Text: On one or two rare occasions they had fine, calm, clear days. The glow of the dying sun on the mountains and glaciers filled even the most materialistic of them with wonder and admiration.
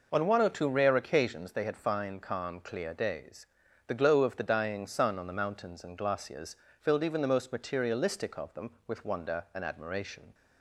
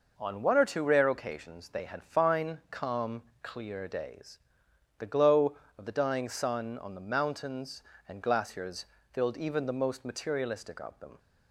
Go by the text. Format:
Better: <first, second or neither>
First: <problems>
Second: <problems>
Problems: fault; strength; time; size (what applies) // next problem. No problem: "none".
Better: first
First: pauses between "glaciers" and "filled"; slight; at 6.5 s; 0.24 s long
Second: pauses between "glaciers" and "filled"; slight; at 8.8 s; 0.26 s long // stops before "with wonder and admiration"; at 11.1 s